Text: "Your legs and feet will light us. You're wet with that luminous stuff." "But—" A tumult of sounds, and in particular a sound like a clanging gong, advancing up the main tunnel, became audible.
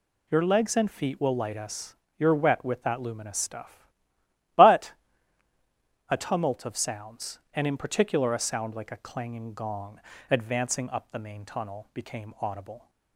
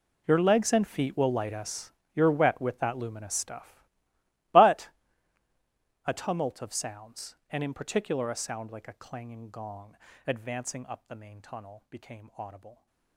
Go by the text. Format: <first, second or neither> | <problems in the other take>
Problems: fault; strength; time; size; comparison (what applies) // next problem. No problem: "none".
first | gets quieter; strong; throughout; 18.5 dB